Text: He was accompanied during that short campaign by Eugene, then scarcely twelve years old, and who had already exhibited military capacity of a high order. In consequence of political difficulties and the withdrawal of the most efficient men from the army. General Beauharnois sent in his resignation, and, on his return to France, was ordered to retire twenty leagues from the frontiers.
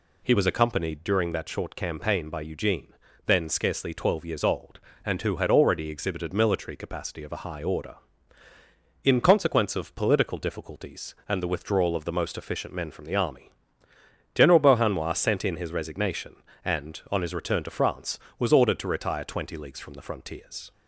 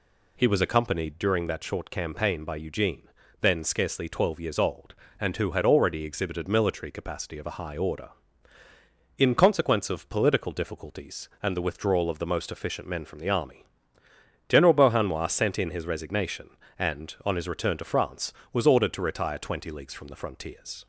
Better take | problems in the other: neither | none

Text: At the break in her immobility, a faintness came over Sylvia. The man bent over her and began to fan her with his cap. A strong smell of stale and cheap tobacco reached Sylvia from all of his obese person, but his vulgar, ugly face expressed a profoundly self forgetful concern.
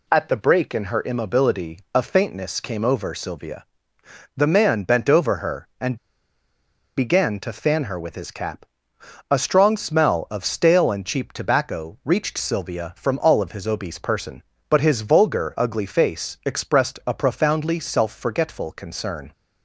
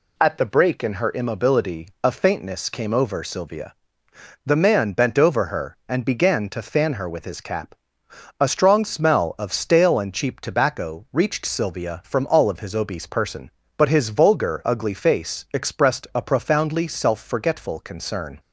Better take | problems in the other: second | pauses between "and" and "began"; at 5.9 s; 0.99 s long

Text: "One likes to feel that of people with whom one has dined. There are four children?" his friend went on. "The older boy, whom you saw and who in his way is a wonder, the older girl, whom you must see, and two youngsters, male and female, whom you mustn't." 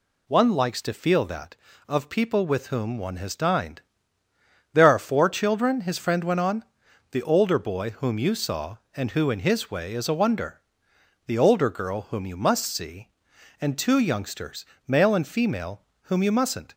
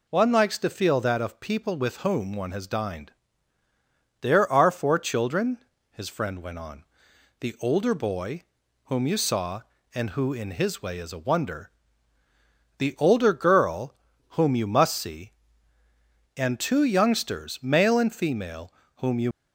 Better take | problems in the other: first | stops before "mustn't"; at 19.3 s

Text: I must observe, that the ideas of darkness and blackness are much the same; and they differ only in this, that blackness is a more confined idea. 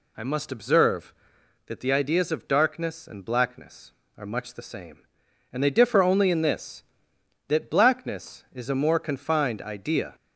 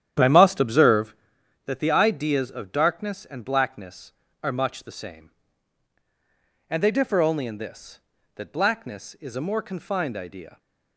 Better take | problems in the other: first | starts louder than the rest; strong; until 1.2 s; 10 dB

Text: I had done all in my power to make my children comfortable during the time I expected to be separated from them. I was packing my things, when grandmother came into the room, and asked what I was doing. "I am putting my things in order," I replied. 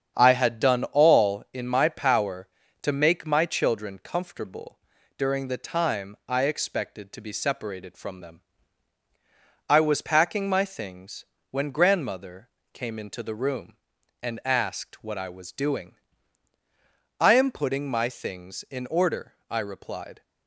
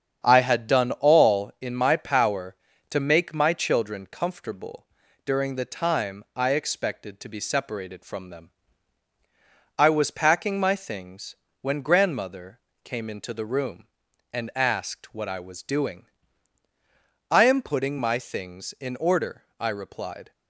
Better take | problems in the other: neither | starts louder than the rest; strong; the same in both // pauses between "comfortable" and "during"; the same in both // pauses between "grandmother" and "came"; slight; the same in both

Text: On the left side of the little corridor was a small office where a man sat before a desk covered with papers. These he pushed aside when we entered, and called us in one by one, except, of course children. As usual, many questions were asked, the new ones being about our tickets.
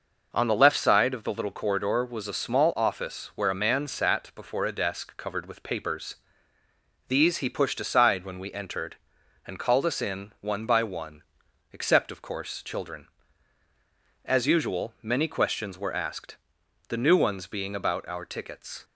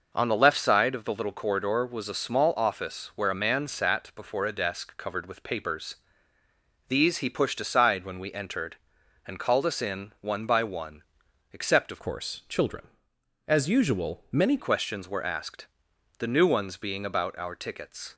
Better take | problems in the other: first | changes voice from "course" to "many"; from 12.0 to 14.5 s; 2.5 s long

